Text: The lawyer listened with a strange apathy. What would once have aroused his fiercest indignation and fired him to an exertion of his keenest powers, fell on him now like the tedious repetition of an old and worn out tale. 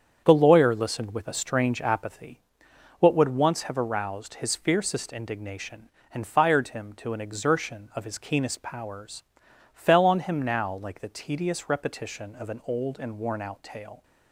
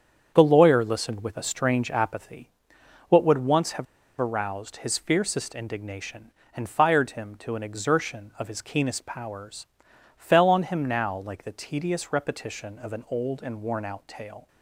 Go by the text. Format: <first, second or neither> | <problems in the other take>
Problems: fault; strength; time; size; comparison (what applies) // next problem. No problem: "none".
first | starts louder than the rest; strong; until 1.3 s; 8 dB; strong in the first // pauses between "have" and "aroused"; slight; at 3.8 s; 0.35 s long